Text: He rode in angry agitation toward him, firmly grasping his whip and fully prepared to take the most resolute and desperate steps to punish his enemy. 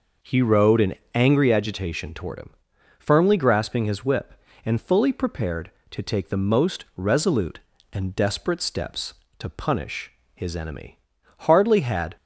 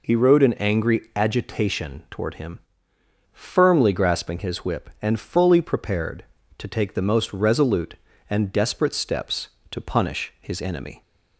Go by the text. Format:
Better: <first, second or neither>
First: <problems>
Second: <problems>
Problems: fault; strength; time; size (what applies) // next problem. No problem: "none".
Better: second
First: pauses between "in" and "angry"; slight; at 0.9 s; 0.20 s long // pauses between "punish" and "his"; slight; at 10.1 s; 0.24 s long // goes on to say "Hardly had"; noticeable; from 11.3 s on; 0.78 s long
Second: none